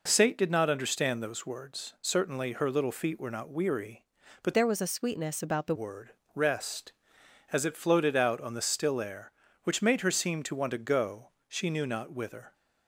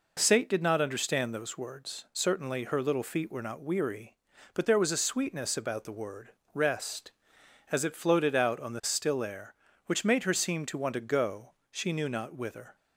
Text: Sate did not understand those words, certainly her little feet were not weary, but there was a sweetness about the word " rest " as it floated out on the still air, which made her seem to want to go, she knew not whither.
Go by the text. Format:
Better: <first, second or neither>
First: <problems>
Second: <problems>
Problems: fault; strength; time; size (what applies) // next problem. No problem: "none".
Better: second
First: changes voice from "there" to "the"; from 4.5 to 5.7 s; 1.2 s long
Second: none